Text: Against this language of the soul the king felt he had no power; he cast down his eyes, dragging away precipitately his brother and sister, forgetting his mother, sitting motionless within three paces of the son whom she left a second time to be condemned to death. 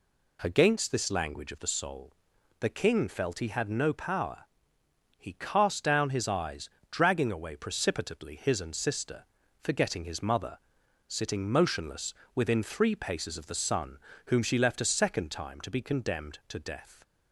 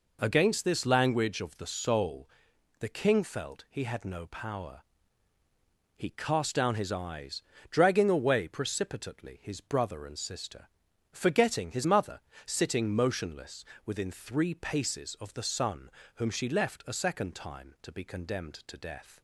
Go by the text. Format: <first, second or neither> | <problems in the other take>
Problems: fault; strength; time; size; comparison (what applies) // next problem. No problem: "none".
second | pauses between "soul" and "the"; noticeable; at 2.1 s; 0.48 s long; noticeable in the second // skips "brother"; at 8.6 s // pauses between "motionless" and "within"; slight; at 12.1 s; 0.22 s long; slight in the second // pauses between "son" and "whom"; slight; at 13.9 s; 0.30 s long; slight in the second